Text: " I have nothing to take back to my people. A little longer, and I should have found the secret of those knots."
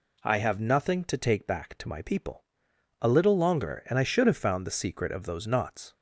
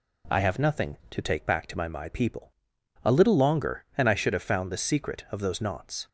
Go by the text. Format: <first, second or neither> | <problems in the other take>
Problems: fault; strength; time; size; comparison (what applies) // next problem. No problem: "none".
first | says "my" twice; at 1.8 s